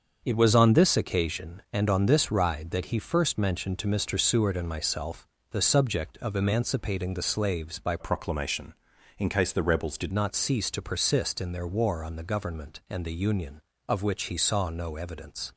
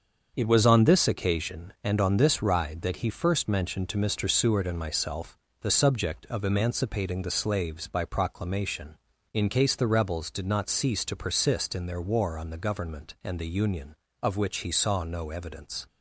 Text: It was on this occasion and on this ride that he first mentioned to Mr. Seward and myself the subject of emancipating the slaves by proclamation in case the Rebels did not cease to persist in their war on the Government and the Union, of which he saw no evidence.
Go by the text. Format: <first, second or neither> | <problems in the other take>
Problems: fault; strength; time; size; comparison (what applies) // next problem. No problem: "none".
second | starts louder than the rest; until 1.2 s; 6.5 dB; also in the second // pauses between "myself" and "the"; slight; at 5.2 s; 0.22 s long; slight in the second // changes voice from "proclamation" to "did"; from 7.9 to 10.1 s; 2.2 s long